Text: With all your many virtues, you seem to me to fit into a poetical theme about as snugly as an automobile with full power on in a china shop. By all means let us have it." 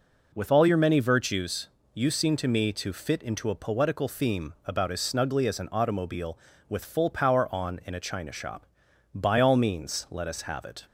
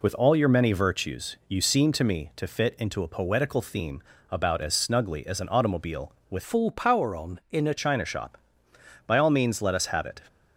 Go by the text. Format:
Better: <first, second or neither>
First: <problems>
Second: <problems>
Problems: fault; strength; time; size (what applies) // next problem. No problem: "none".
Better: first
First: none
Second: pauses between "theme" and "about"; slight; at 4.0 s; 0.30 s long // changes voice from "full" to "a"; from 6.4 to 7.7 s; 1.3 s long